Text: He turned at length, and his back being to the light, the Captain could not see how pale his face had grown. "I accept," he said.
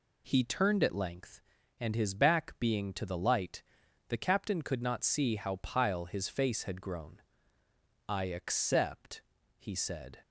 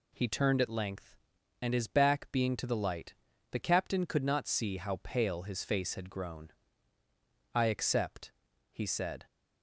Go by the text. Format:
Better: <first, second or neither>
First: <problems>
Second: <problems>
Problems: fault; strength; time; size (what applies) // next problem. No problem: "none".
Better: second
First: says "pile" for "pale"; at 5.5 s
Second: none